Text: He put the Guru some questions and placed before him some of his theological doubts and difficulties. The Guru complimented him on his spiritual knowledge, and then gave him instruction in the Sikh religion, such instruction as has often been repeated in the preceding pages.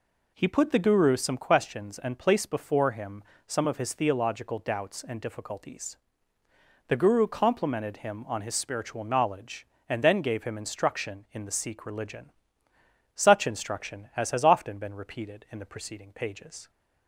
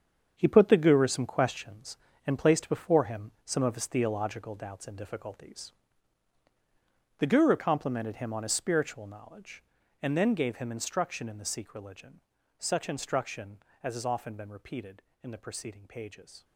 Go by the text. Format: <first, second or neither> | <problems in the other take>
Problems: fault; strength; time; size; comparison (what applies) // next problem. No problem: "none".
first | gets quieter; strong; throughout; 10.5 dB // pauses between "him" and "some"; slight; at 3.3 s; 0.16 s long; slight in the first